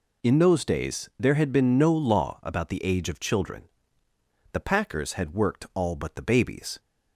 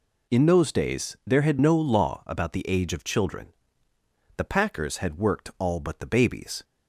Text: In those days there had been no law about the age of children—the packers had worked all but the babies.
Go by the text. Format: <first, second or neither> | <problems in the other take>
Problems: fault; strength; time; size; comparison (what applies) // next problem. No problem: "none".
first | skips "been"; at 1.5 s